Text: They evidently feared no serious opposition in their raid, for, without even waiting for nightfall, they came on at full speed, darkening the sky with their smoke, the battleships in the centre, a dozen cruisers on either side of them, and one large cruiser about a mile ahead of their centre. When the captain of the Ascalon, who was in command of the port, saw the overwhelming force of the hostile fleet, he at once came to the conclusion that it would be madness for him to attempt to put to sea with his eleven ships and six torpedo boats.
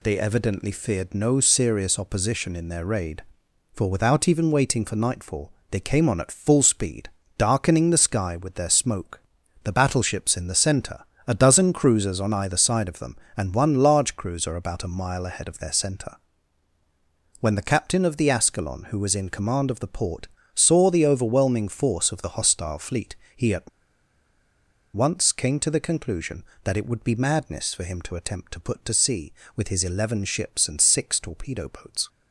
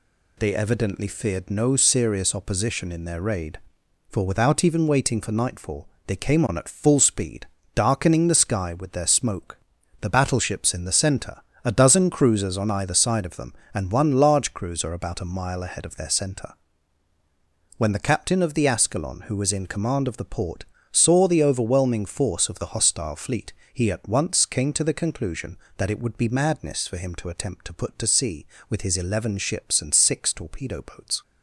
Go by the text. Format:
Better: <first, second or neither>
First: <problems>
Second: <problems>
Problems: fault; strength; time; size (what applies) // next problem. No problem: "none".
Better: second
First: pauses between "at" and "once"; at 23.6 s; 1.2 s long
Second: none